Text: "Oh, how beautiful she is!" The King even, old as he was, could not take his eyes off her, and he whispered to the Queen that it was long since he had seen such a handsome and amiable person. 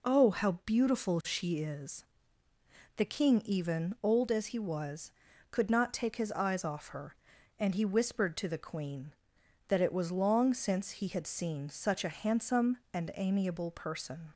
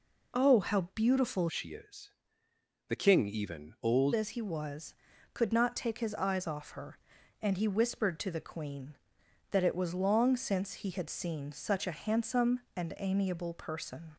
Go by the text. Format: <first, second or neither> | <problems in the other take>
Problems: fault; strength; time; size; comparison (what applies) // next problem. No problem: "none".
first | changes voice from "she" to "old"; from 1.4 to 4.1 s; 2.7 s long